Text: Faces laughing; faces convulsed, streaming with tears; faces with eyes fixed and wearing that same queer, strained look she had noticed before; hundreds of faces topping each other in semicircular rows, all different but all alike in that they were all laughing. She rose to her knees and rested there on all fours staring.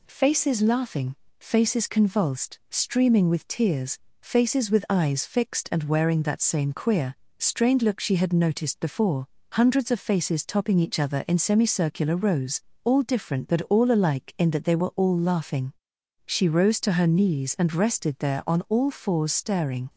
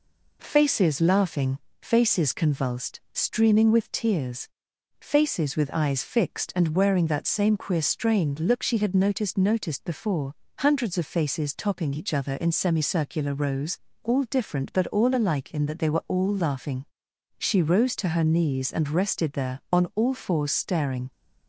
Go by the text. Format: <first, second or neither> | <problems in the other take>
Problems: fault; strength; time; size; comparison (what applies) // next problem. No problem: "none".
first | says "noticed" twice; at 9.3 s